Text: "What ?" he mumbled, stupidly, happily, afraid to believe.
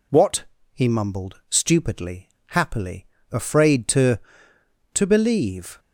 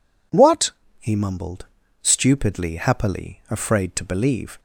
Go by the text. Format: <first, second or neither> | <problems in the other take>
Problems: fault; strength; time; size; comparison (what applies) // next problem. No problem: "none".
second | says "to" twice; at 4.9 s